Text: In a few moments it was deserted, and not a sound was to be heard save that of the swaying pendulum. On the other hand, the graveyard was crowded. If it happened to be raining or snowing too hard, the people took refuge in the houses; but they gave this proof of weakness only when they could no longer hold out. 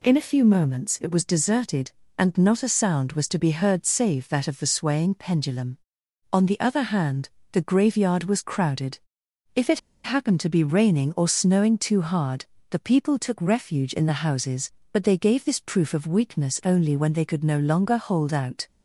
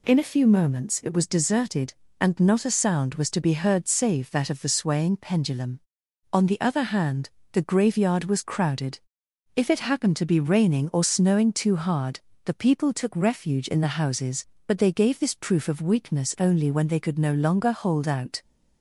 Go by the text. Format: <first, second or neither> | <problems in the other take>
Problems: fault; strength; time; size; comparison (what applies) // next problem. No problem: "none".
second | pauses between "it" and "happened"; slight; at 9.7 s; 0.25 s long